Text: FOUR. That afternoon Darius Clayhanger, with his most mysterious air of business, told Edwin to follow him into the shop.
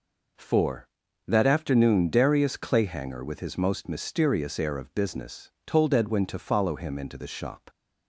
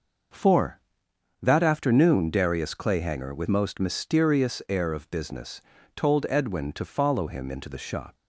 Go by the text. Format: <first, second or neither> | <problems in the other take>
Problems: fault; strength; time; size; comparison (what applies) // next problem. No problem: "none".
first | skips "his"; at 3.4 s